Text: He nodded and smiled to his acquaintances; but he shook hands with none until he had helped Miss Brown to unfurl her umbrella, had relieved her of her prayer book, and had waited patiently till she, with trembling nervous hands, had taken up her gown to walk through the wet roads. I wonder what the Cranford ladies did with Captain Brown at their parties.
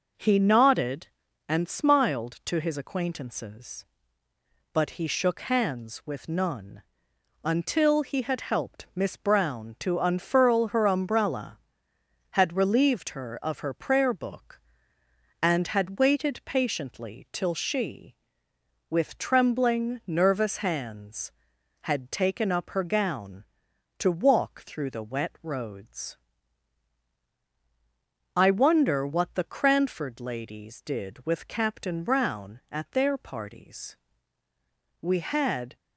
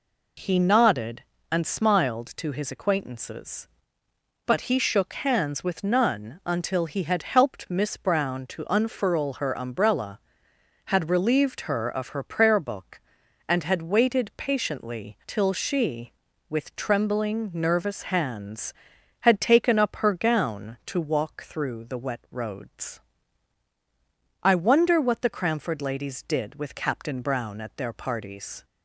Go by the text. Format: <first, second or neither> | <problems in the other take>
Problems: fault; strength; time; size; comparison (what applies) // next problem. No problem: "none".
second | pauses between "none" and "until"; noticeable; at 6.8 s; 0.62 s long // goes on to say "We had"; noticeable; from 34.9 s on; 0.76 s long